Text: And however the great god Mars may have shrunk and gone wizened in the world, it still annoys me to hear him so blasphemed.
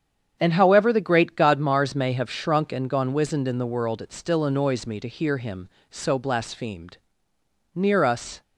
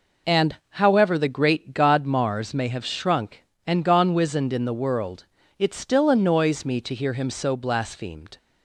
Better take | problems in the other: second | starts louder than the rest; strong; until 1.4 s; 8 dB // goes on to say "Near us"; noticeable; from 7.7 s on; 0.68 s long

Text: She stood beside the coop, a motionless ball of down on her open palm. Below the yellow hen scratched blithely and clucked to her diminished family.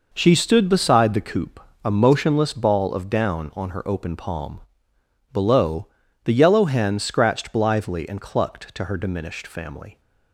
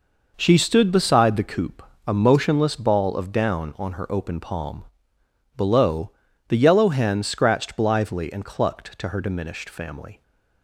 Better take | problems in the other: neither | pauses between "Below" and "the"; the same in both

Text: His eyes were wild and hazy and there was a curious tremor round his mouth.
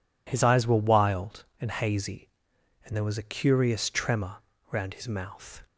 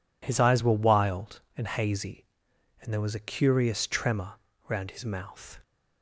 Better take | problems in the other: neither | pauses between "tremor" and "round"; slight; the same in both

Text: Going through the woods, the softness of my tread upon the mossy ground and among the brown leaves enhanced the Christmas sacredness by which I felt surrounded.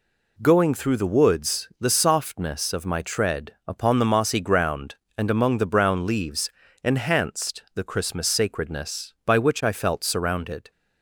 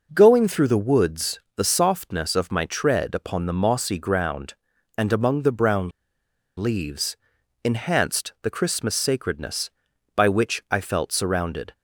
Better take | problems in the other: first | pauses between "brown" and "leaves"; noticeable; at 5.8 s; 0.68 s long // pauses between "leaves" and "enhanced"; noticeable; at 7.1 s; 0.48 s long; slight in the first

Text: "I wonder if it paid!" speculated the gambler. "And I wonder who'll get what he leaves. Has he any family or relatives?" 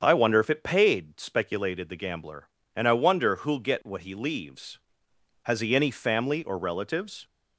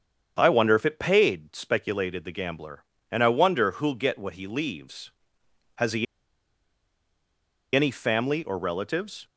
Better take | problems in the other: first | starts louder than the rest; strong; until 1.3 s; 7.5 dB; strong in the first // pauses between "he" and "any"; strong; at 6.0 s; 1.7 s long

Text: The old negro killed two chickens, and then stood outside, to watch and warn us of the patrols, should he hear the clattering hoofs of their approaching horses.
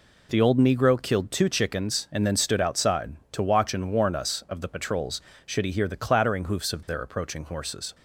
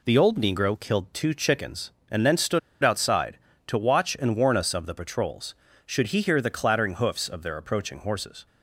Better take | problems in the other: first | pauses between "stood" and "outside"; slight; at 2.5 s; 0.23 s long

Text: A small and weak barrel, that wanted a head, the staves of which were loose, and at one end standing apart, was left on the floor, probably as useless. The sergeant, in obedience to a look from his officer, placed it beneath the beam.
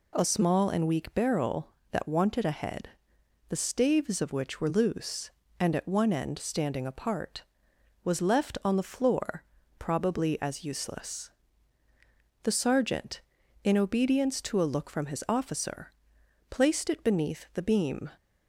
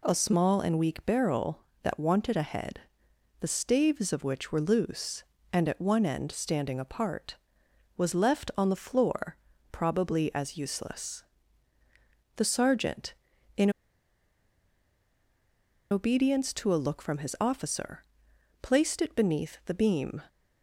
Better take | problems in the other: first | pauses between "in" and "obedience"; strong; at 13.6 s; 2.2 s long

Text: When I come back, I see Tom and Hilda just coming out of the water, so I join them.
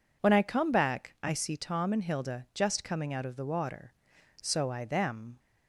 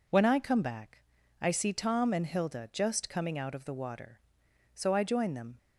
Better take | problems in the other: second | skips "join"; at 4.8 s

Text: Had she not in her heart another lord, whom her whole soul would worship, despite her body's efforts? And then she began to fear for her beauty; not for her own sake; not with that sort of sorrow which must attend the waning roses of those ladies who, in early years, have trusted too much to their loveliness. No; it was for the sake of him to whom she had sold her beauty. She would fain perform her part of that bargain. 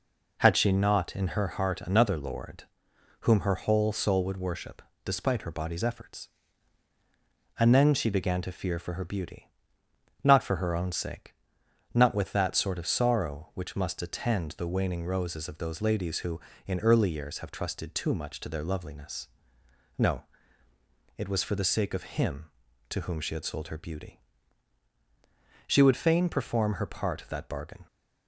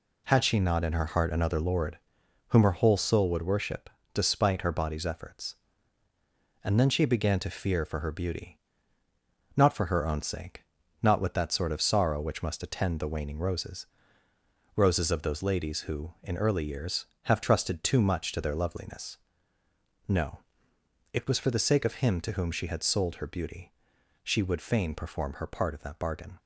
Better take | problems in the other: first | says "roses" twice; at 14.7 s

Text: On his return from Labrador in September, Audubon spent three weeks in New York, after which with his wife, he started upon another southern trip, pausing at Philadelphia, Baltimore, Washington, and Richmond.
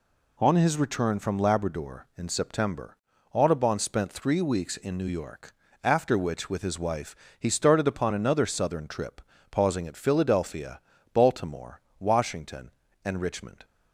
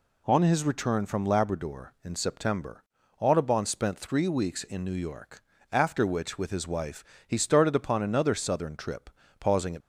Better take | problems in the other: first | stops before "Philadelphia Baltimore Washington and Richmond"; at 9.8 s

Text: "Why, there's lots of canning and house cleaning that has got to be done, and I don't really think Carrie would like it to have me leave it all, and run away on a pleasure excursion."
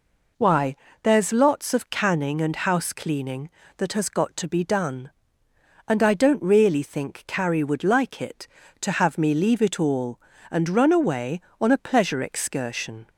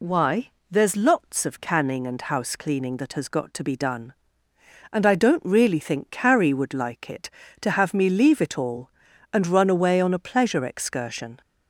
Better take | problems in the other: neither | none

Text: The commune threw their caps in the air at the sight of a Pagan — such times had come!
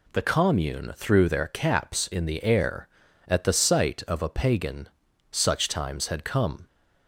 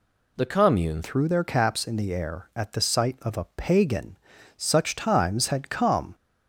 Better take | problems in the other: first | changes voice at "threw"; from 1.0 s on; 5.1 s long

